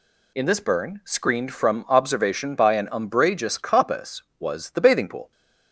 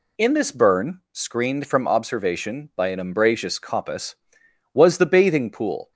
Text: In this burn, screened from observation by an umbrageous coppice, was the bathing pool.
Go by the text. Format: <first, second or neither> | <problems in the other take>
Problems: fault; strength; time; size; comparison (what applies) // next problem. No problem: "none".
neither | none